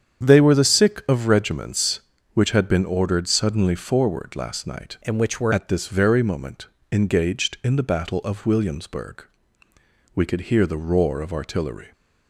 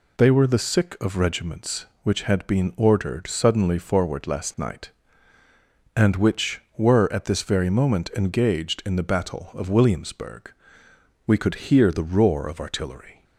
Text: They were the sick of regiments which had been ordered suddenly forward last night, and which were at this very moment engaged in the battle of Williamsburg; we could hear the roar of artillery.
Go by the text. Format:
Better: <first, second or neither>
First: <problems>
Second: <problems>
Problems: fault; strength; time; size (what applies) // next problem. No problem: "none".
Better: second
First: starts louder than the rest; strong; until 1.2 s; 8 dB // changes voice from "and" to "were"; from 5.0 to 5.5 s; 0.5 s long // pauses between "moment" and "engaged"; slight; at 6.6 s; 0.26 s long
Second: none